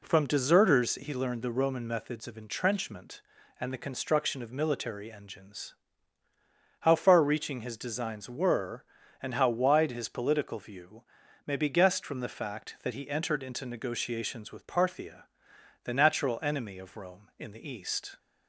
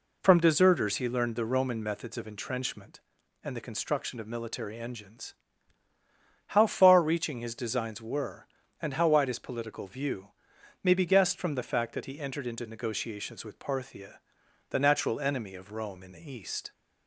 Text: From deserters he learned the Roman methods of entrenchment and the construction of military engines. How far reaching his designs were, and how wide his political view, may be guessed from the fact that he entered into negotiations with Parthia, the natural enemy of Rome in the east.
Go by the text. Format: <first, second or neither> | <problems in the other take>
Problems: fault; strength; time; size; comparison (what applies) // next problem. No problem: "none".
neither | none